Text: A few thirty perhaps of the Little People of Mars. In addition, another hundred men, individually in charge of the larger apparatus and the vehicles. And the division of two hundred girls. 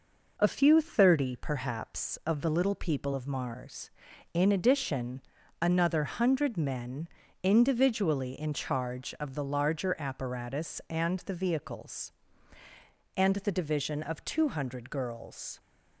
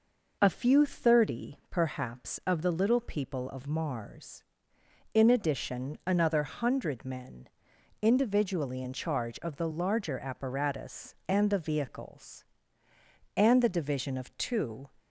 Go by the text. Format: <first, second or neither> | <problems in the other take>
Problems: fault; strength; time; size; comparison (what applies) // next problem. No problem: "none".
first | stops before "hundred girls"; at 14.9 s